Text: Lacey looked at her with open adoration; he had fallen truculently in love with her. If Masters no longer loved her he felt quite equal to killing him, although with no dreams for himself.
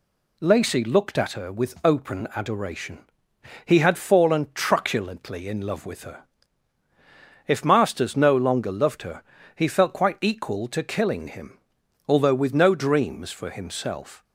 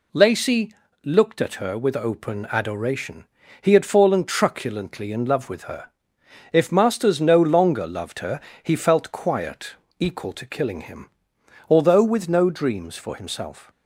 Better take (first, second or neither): first